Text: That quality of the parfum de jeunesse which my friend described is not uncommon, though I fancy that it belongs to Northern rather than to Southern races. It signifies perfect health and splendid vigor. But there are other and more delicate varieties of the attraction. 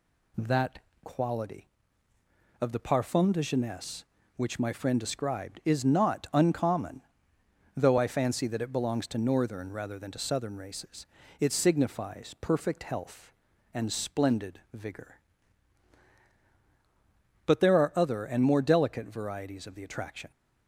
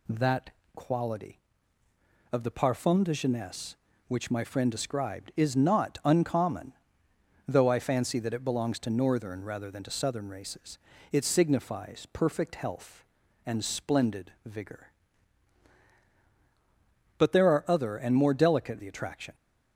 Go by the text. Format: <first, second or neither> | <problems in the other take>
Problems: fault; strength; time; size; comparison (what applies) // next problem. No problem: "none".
first | pauses between "That" and "quality"; slight; at 0.5 s; 0.24 s long; slight in the first // skips "varieties of"; at 18.7 s